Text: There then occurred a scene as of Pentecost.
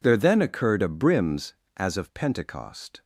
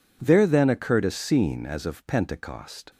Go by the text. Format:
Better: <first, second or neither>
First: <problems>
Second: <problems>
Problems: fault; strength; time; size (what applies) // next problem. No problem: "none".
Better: second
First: says "brims" for "scene"; at 0.8 s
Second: none